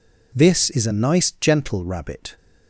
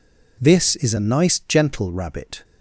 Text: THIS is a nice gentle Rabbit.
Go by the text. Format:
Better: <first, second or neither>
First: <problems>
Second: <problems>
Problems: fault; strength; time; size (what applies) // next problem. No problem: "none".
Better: neither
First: none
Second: none